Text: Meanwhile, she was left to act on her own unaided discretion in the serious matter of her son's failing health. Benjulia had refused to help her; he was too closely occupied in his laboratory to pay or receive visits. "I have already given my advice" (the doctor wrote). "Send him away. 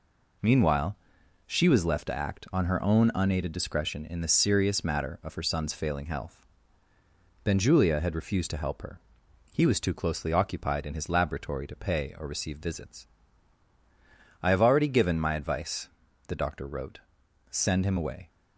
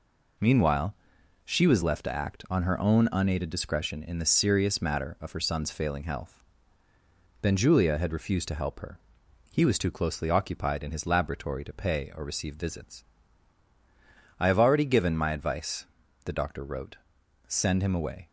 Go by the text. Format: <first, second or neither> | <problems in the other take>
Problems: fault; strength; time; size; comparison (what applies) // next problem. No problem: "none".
neither | none